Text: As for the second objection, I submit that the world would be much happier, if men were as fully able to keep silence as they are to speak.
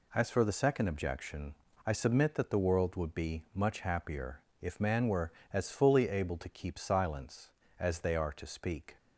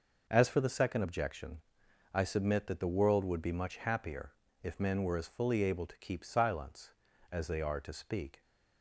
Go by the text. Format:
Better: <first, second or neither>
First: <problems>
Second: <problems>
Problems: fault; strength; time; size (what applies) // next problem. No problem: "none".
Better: second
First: says "man" for "men"; at 4.8 s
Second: none